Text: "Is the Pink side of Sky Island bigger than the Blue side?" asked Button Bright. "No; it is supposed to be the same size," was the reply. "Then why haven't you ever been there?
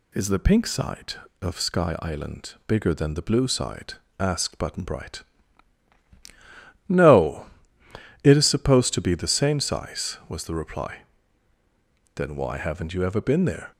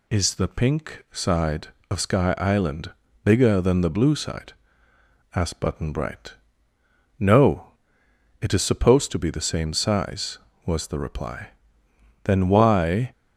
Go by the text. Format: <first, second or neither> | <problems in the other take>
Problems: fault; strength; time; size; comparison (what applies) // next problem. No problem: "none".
first | pauses between "Island" and "bigger"; slight; at 2.9 s; 0.34 s long // stops before "haven't you ever been there"; at 13.1 s